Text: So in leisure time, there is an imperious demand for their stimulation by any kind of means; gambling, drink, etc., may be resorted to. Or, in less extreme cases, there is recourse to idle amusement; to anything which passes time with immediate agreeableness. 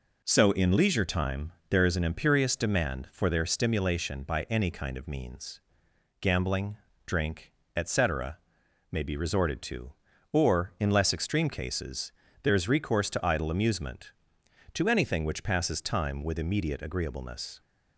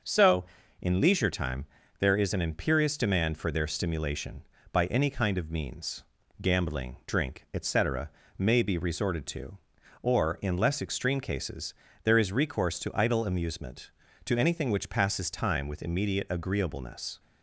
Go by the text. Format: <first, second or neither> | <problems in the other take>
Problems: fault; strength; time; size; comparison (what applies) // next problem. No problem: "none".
neither | none